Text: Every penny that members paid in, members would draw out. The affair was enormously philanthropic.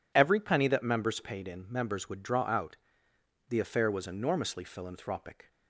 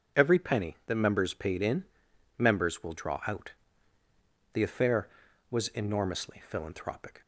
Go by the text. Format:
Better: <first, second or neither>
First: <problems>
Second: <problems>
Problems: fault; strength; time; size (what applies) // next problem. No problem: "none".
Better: first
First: none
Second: says "will" for "would"; at 2.8 s